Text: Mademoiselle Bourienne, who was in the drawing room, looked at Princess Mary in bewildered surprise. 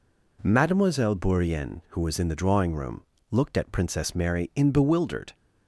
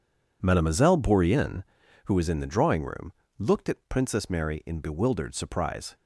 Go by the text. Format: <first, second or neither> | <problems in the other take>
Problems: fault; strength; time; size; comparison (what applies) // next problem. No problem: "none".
second | stops before "surprise"; at 5.3 s